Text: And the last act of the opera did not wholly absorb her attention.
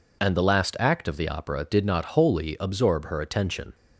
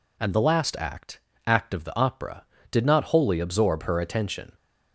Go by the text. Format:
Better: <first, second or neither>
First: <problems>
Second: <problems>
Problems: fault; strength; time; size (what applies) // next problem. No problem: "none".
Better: first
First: none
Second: says "act" twice; at 1.4 s